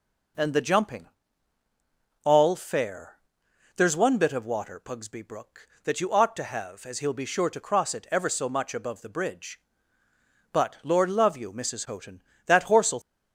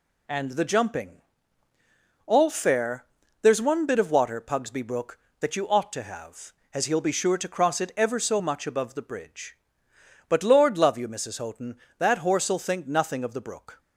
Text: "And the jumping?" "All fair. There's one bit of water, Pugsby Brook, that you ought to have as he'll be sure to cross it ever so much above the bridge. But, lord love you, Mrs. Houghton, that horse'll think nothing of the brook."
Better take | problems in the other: second | stops before "think nothing of the brook"; at 13.0 s

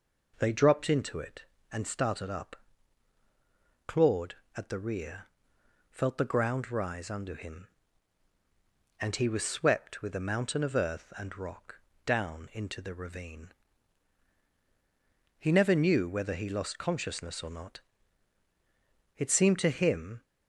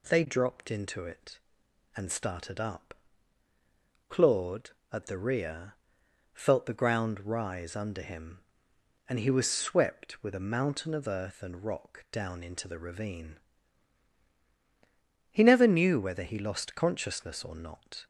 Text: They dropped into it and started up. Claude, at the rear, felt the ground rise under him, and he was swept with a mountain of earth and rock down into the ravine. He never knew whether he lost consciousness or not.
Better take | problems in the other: second | pauses between "rock" and "down"; slight; at 11.7 s; 0.26 s long // goes on to say "It seemed to him"; noticeable; from 19.1 s on; 1.0 s long

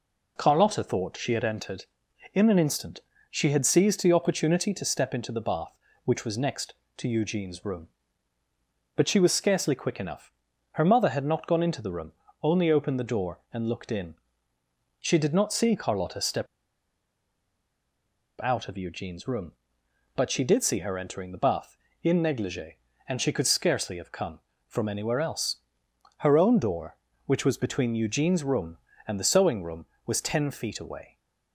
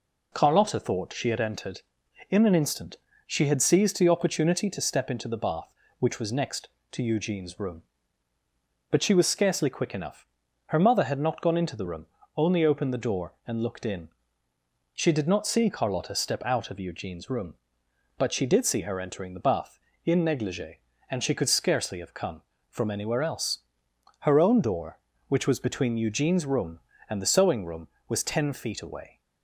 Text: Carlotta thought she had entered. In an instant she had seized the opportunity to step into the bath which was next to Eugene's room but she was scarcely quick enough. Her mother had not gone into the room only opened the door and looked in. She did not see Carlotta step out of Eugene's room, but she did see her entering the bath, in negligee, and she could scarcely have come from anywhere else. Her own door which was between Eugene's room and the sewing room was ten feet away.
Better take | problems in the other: second | pauses between "instant" and "she"; slight; at 2.9 s; 0.30 s long; slight in the second // pauses between "room" and "only"; slight; at 12.1 s; 0.30 s long; slight in the second // pauses between "step" and "out"; strong; at 16.4 s; 1.9 s long

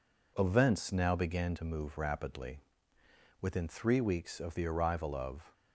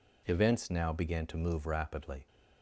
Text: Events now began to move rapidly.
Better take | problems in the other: second | goes on to say "Within three weeks of the arrival of"; strong; from 3.4 s on; 2.1 s long

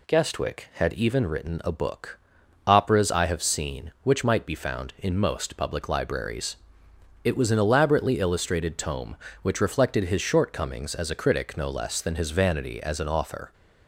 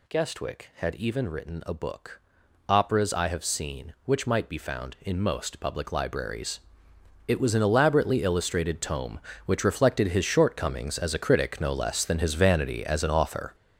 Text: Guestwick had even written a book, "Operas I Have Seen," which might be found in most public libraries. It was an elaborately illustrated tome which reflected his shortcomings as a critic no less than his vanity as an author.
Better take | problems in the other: first | gets louder; strong; throughout; 9 dB

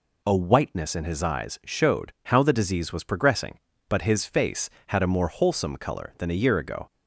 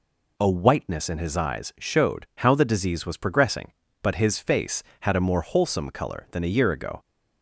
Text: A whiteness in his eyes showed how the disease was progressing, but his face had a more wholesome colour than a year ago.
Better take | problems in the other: neither | none

